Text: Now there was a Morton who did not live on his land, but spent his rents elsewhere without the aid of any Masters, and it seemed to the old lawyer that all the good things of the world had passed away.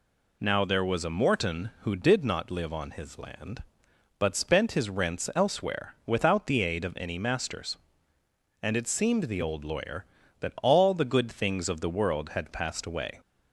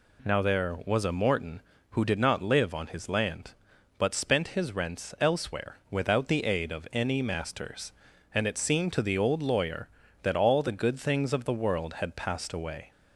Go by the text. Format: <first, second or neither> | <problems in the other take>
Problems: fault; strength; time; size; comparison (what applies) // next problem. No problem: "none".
second | skips "to"; at 9.2 s